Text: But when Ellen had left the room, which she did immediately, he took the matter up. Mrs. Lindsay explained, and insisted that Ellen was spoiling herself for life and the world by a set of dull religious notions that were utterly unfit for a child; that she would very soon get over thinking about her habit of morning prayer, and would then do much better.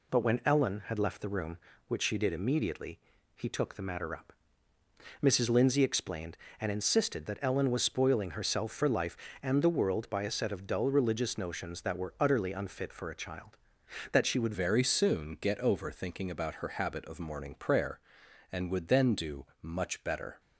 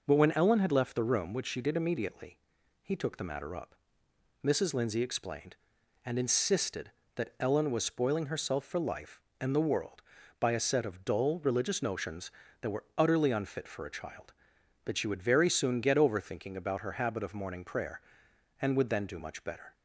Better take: second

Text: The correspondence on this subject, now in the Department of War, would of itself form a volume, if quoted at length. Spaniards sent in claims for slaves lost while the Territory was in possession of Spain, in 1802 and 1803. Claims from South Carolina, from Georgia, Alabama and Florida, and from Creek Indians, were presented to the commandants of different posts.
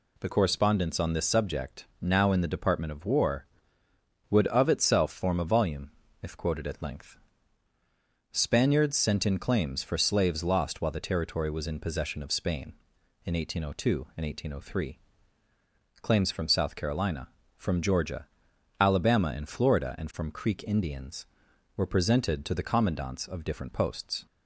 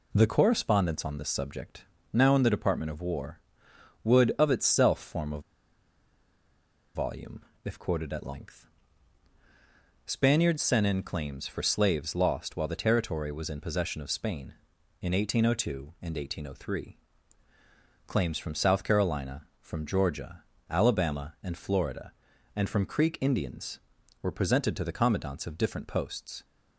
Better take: first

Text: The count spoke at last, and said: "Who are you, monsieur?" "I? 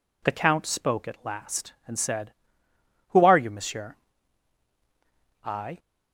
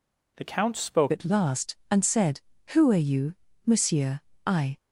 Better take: first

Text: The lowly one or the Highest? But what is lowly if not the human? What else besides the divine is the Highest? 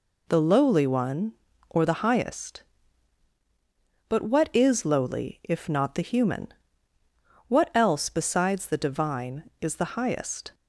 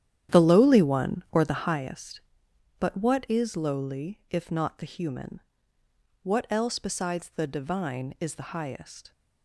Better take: first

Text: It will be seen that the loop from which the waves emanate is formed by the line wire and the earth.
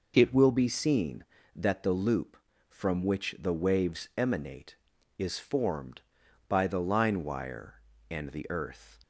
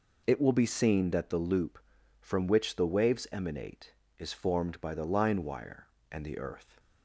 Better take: neither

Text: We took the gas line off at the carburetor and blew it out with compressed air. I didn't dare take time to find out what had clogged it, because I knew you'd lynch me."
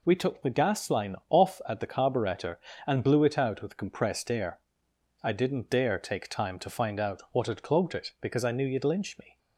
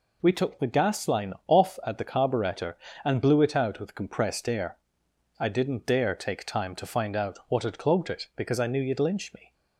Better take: neither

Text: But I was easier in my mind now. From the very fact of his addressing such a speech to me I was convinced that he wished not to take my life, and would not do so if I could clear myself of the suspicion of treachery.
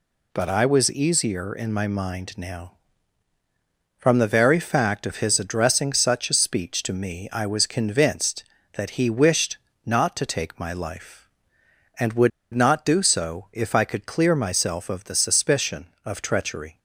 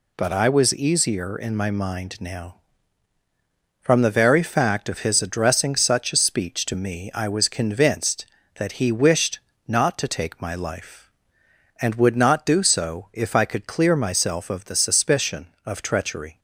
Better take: second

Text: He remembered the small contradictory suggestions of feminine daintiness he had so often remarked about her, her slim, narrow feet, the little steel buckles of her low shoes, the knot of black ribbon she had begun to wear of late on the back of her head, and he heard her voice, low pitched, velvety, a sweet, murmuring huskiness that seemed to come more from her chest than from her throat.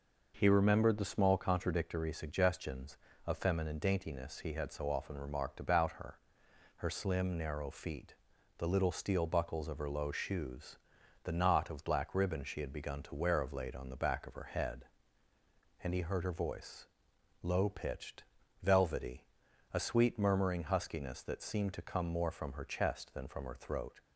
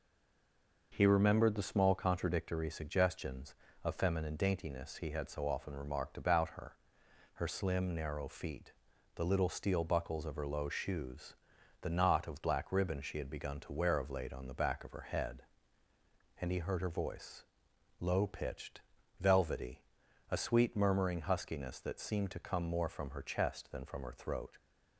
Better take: first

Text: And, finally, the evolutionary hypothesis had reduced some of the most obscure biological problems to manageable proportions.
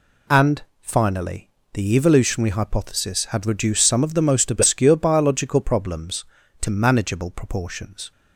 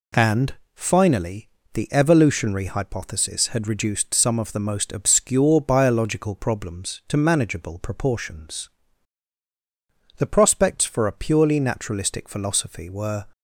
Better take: first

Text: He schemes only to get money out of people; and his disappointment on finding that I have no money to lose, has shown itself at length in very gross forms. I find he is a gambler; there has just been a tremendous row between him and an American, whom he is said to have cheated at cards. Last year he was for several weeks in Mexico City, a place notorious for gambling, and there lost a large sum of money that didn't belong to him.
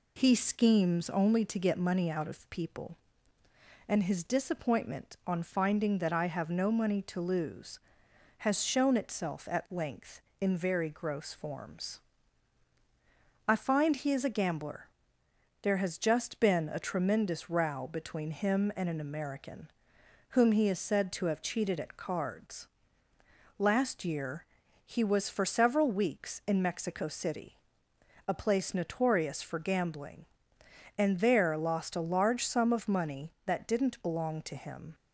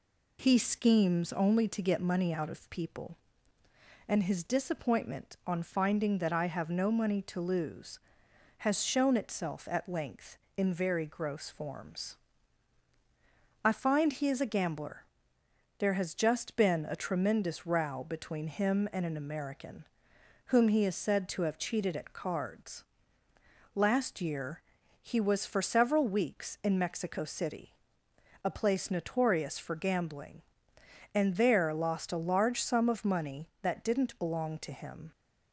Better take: neither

